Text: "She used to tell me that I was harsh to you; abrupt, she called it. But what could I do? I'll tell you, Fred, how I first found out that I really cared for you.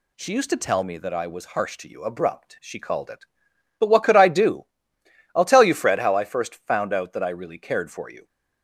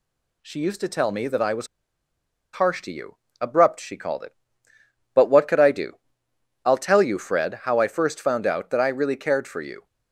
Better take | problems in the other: first | pauses between "was" and "harsh"; noticeable; at 1.6 s; 0.86 s long

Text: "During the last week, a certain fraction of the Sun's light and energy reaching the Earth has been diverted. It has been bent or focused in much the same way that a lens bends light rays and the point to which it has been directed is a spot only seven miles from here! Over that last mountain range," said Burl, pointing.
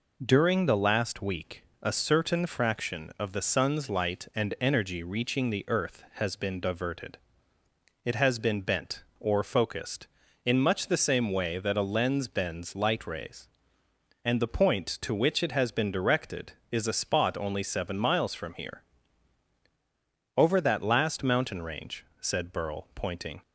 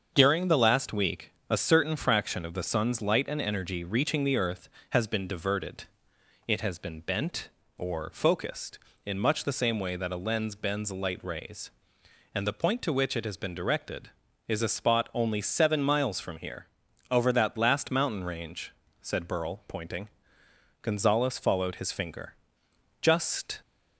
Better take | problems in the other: first | starts louder than the rest; until 1.1 s; 7 dB // goes on to say "Gonzales followed his finger Just"; strong; from 20.8 s on; 2.8 s long

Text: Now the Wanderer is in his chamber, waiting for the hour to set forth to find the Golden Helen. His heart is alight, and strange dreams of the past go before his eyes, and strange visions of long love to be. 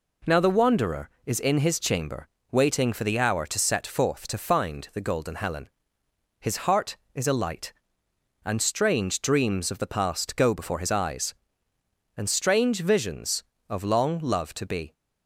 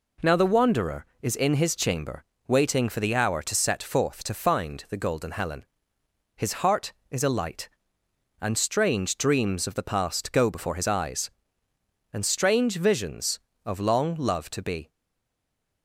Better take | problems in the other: first | stays silent after the last word; from 14.8 s on; 1.0 s long

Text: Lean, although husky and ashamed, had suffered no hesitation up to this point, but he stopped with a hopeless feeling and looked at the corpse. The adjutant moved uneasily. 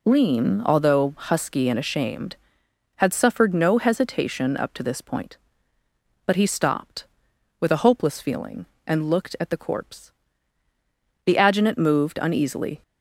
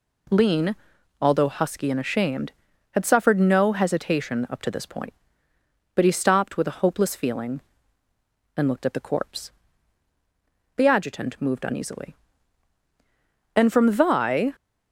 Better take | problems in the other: first | goes on to say "And from Thy"; noticeable; from 13.5 s on; 0.98 s long

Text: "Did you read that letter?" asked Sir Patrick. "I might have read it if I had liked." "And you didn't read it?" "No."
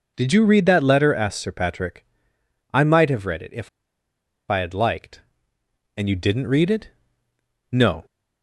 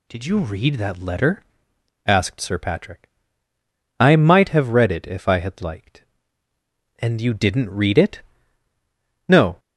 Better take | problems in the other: second | pauses between "if" and "I"; noticeable; at 3.6 s; 0.82 s long

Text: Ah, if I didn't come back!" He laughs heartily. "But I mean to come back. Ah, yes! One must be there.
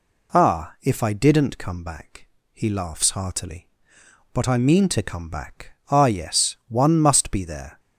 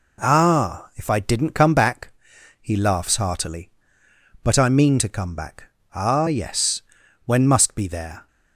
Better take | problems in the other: first | says "When" for "One"; at 7.2 s

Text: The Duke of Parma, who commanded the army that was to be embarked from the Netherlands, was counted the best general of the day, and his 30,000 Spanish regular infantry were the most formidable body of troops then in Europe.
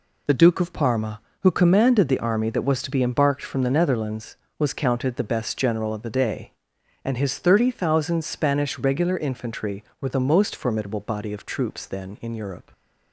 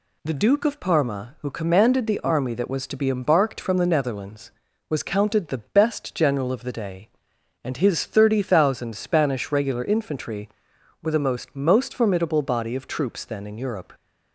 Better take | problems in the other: first | says "most" twice; at 11.5 s

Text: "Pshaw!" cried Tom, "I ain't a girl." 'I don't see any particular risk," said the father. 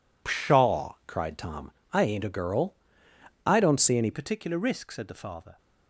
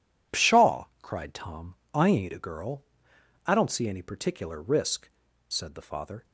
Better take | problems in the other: second | changes voice at "particular"; from 4.1 s on; 1.4 s long

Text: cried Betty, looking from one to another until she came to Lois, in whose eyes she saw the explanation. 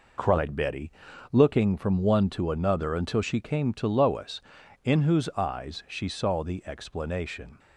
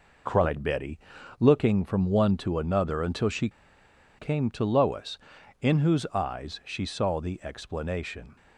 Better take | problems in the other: first | pauses between "she" and "came"; noticeable; at 3.4 s; 0.70 s long

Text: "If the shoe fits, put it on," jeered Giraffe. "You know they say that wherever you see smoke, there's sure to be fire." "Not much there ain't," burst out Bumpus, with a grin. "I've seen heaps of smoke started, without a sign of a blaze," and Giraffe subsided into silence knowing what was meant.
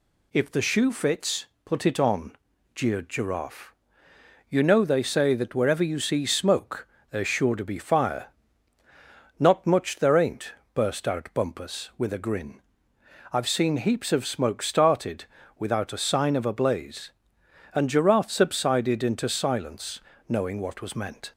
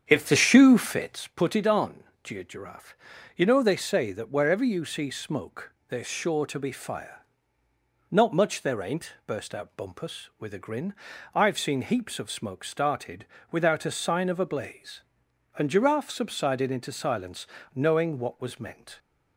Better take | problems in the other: first | starts louder than the rest; strong; until 1.3 s; 8 dB // pauses between "silence" and "knowing"; slight; at 17.4 s; 0.26 s long; slight in the first

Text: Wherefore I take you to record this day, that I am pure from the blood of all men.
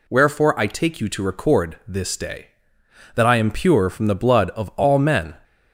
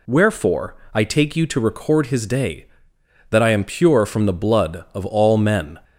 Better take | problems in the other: first | pauses between "Wherefore" and "I"; slight; at 0.7 s; 0.18 s long // says "his" for "this"; at 2.0 s

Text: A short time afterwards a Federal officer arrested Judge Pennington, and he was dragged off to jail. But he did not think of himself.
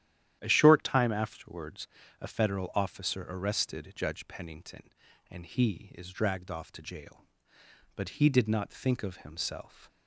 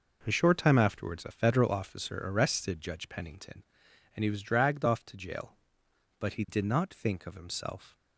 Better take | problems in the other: second | starts louder than the rest; strong; until 1.4 s; 11 dB // pauses between "afterwards" and "a"; slight; at 1.8 s; 0.34 s long // says "is" for "was"; at 5.9 s

